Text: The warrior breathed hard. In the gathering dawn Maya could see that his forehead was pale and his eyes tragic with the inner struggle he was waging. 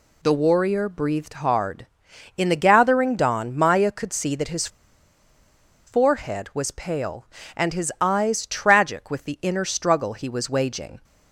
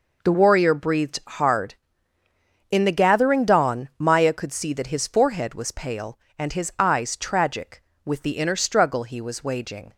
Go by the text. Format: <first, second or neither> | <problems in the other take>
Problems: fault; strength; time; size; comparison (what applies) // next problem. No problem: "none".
second | pauses between "his" and "forehead"; at 4.6 s; 1.1 s long